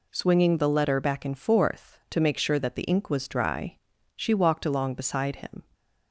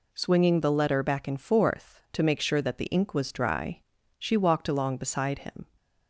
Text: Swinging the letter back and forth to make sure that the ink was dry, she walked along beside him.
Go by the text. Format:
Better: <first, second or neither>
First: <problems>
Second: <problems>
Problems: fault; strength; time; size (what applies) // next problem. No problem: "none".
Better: neither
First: none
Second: none